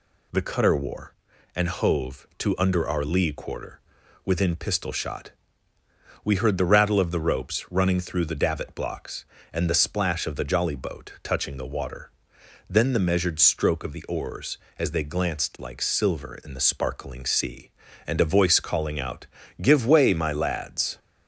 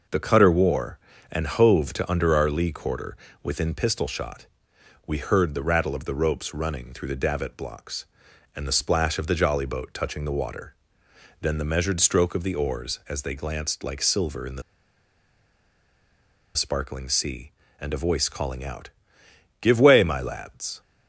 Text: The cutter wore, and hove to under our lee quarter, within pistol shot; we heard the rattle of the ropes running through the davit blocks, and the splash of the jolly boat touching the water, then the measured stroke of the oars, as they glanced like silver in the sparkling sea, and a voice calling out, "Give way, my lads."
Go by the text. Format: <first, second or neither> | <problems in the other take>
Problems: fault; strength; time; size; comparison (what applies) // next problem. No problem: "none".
first | pauses between "the" and "sparkling"; strong; at 14.6 s; 1.9 s long